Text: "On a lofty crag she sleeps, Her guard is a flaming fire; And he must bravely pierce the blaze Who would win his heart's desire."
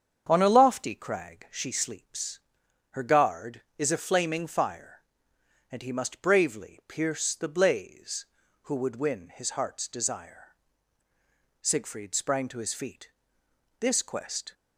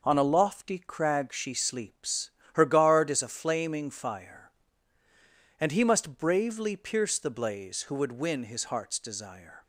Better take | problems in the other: second | starts louder than the rest; strong; until 1.3 s; 7.5 dB // goes on to say "Siegfried sprang to his feet This quest"; strong; from 11.6 s on; 2.9 s long

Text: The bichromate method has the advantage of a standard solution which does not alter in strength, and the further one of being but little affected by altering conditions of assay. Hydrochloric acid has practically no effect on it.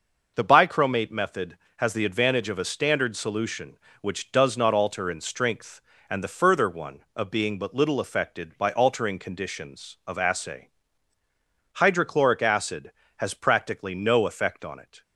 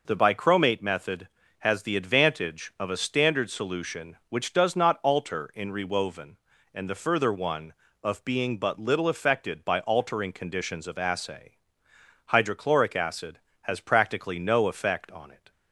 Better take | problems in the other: first | says "rewoven" for "strength"; at 5.7 s

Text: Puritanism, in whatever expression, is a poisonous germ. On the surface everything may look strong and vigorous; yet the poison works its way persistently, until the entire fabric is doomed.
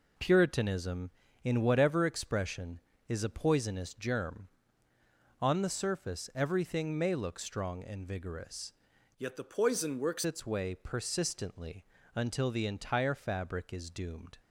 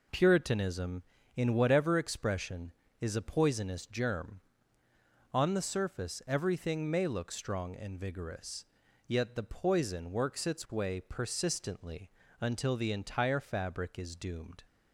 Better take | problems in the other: second | changes voice from "yet" to "works"; from 9.1 to 10.2 s; 1.1 s long

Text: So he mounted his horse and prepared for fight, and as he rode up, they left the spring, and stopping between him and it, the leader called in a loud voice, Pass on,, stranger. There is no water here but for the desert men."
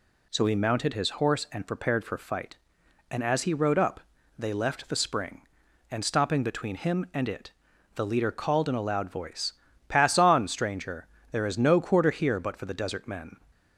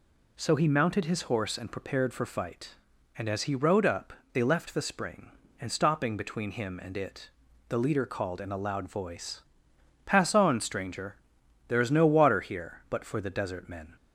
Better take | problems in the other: second | says "quarter" for "water"; at 11.8 s

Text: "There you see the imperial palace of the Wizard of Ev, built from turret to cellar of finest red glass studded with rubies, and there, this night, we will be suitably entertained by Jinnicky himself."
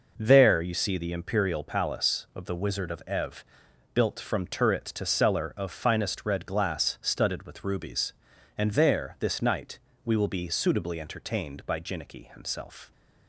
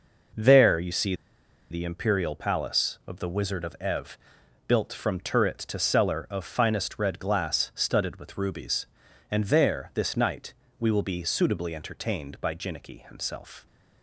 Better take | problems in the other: first | pauses between "see" and "the"; noticeable; at 1.1 s; 0.56 s long

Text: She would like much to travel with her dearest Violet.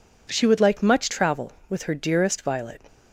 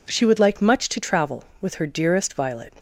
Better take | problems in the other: second | skips "to"; at 1.0 s

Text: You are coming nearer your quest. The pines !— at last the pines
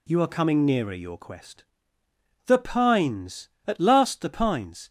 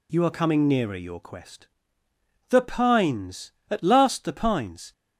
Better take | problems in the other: neither | none

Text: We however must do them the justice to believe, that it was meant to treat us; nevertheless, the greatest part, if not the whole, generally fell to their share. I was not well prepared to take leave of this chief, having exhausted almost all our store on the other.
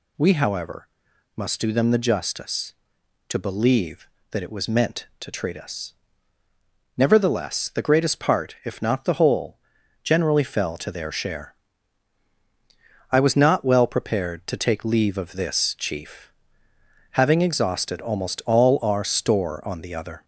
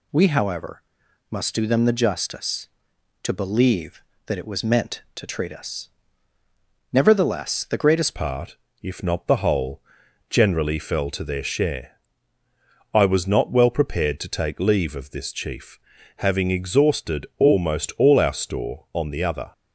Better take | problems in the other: first | pauses between "however" and "must"; noticeable; at 0.8 s; 0.48 s long; noticeable in the first // changes voice at "part"; from 8.1 s on; 11.4 s long

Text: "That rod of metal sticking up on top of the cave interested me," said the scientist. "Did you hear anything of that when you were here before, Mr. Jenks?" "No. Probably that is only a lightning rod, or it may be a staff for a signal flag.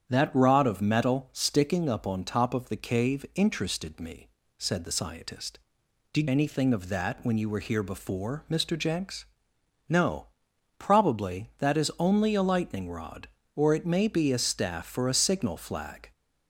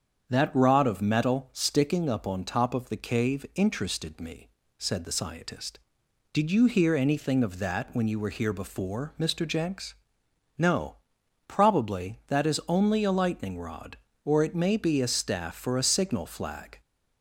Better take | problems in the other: second | starts louder than the rest; strong; until 1.0 s; 8.5 dB; strong in the second // skips "you hear"; at 6.2 s

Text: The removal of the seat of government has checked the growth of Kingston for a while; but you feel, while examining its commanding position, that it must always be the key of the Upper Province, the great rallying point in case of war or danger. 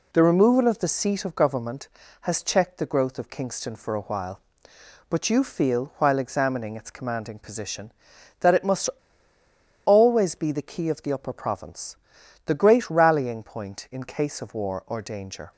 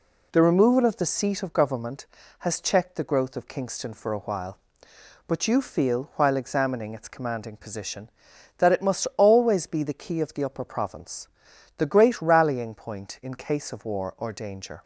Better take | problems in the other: second | pauses between "must" and "always"; noticeable; at 8.8 s; 0.96 s long

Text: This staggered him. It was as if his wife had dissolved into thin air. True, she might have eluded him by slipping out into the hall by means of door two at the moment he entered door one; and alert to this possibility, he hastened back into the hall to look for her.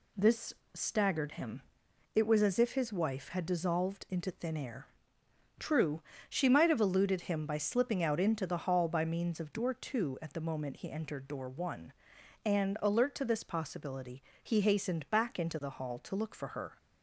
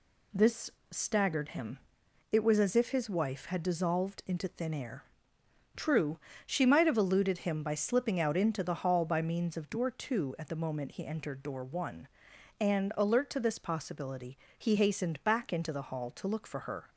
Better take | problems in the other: neither | pauses between "This" and "staggered"; slight; the same in both

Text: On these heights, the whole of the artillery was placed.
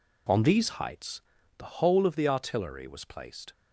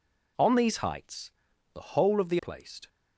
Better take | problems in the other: first | skips "artillery was"; at 2.3 s

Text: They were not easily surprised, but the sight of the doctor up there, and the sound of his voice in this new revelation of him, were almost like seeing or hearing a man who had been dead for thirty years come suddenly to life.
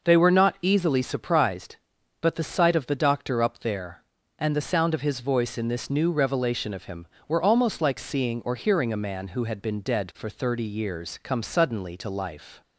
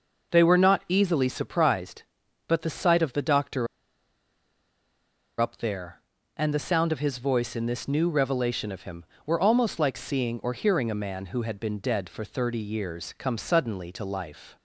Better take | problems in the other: first | pauses between "doctor" and "up"; strong; at 3.6 s; 1.7 s long

